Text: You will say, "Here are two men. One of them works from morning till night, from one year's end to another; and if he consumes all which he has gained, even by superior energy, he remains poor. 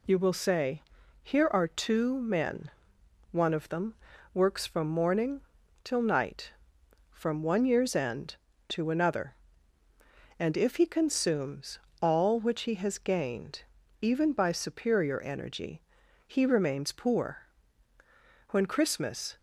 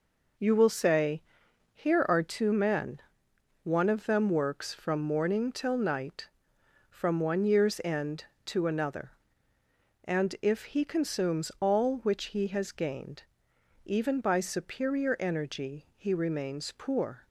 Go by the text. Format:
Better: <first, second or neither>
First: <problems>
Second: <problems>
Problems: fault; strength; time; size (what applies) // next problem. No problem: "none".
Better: second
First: pauses between "them" and "works"; at 3.9 s; 0.38 s long // pauses between "morning" and "till"; at 5.4 s; 0.42 s long // pauses between "consumes" and "all"; slight; at 11.7 s; 0.24 s long // goes on to say "When Christmas"; noticeable; from 18.4 s on; 0.88 s long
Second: none